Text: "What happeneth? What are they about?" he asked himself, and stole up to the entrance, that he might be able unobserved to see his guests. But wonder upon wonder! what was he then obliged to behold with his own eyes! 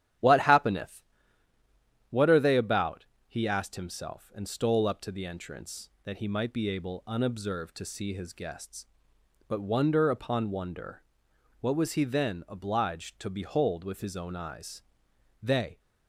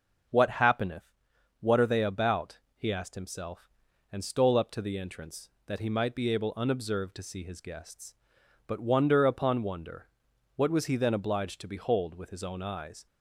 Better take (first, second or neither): second